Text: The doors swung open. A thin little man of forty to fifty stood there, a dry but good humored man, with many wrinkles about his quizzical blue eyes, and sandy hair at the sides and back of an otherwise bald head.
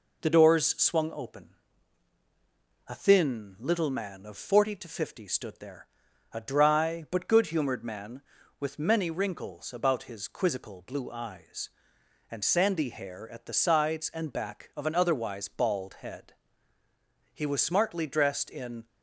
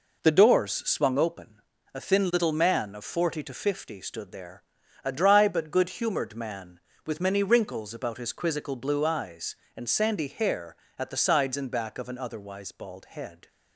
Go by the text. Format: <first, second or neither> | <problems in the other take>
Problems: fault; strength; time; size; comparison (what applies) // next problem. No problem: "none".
second | goes on to say "He was smartly dressed in"; from 17.3 s on; 1.5 s long